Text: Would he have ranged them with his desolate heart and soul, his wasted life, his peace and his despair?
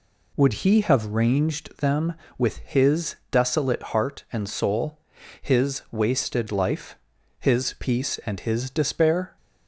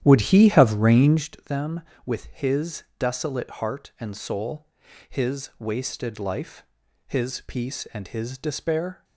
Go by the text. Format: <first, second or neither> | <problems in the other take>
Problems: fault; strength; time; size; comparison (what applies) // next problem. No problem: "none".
first | starts louder than the rest; strong; until 1.3 s; 11 dB